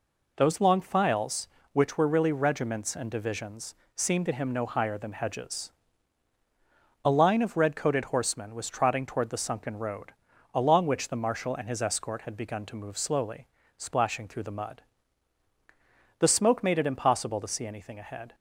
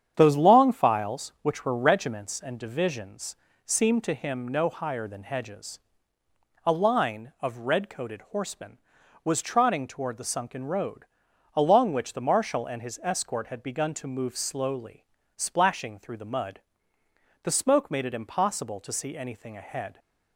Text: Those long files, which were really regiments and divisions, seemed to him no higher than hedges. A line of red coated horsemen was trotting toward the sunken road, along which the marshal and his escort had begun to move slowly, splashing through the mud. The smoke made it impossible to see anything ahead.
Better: first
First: none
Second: starts louder than the rest; strong; until 1.1 s; 8.5 dB // skips "really"; at 1.7 s

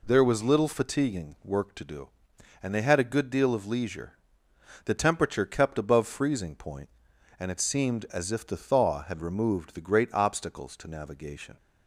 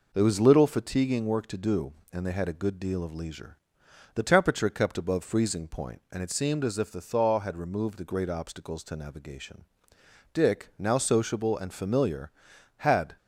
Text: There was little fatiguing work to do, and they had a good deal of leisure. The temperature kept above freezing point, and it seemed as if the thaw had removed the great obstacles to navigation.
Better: first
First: none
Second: goes on to say "Dick now sociable and familiar had"; strong; from 10.3 s on; 2.8 s long

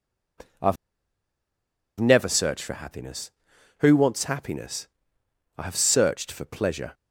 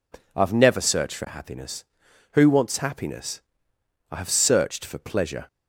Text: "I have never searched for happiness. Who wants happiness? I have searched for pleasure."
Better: second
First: pauses between "have" and "never"; at 0.7 s; 1.2 s long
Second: none

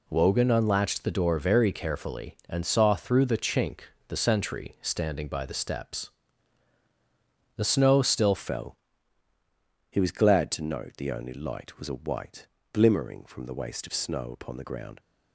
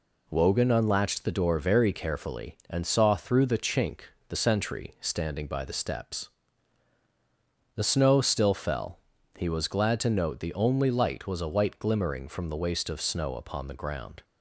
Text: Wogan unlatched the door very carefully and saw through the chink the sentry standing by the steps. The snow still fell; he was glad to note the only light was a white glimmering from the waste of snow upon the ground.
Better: second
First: pauses between "chink" and "the"; slight; at 3.8 s; 0.26 s long // changes voice at "fell"; from 8.3 s on; 6.6 s long // pauses between "white" and "glimmering"; slight; at 12.4 s; 0.26 s long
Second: pauses between "chink" and "the"; slight; at 4.0 s; 0.26 s long

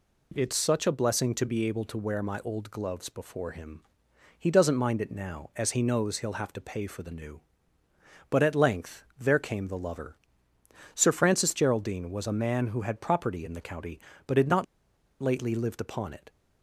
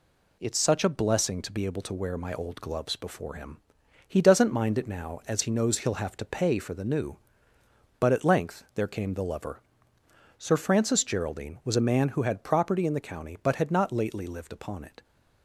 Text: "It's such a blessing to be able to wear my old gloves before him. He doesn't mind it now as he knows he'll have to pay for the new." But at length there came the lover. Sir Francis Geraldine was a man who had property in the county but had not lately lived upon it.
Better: second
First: pauses between "not" and "lately"; noticeable; at 14.6 s; 0.55 s long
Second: none

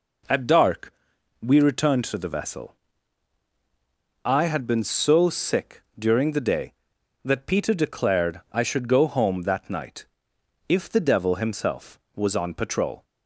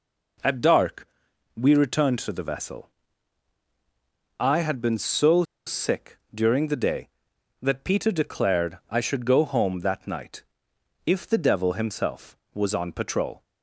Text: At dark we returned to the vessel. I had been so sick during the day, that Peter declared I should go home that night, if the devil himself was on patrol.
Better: first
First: pauses between "dark" and "we"; noticeable; at 0.9 s; 0.52 s long // pauses between "sick" and "during"; slight; at 5.8 s; 0.16 s long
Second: pauses between "dark" and "we"; noticeable; at 1.0 s; 0.52 s long // pauses between "so" and "sick"; slight; at 5.4 s; 0.23 s long // pauses between "sick" and "during"; slight; at 6.1 s; 0.16 s long

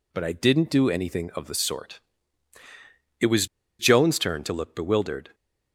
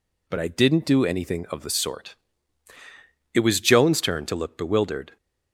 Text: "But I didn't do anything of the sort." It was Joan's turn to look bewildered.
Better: second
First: pauses between "was" and "Joan's"; slight; at 3.4 s; 0.34 s long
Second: none

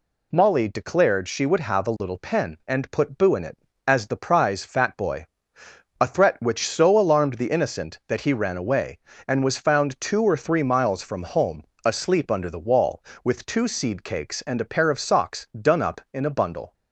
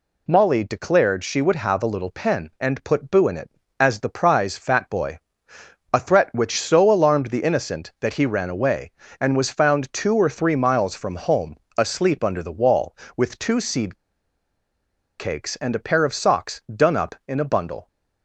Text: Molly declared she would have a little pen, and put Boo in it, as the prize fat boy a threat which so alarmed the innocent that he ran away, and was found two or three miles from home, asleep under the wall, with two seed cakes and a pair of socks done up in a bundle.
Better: first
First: pauses between "boy" and "a"; noticeable; at 5.2 s; 0.74 s long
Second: pauses between "boy" and "a"; noticeable; at 5.1 s; 0.74 s long // pauses between "seed" and "cakes"; at 13.9 s; 1.2 s long

